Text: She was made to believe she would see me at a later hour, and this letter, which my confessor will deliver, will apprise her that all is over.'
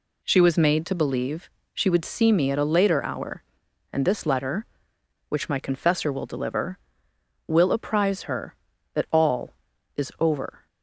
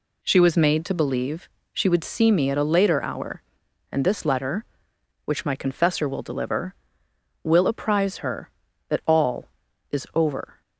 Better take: neither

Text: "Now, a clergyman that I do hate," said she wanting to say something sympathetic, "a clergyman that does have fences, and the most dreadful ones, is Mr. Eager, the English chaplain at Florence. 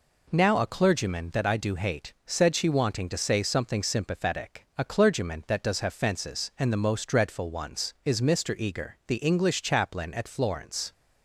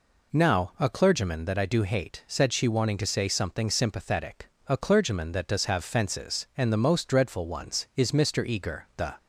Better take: first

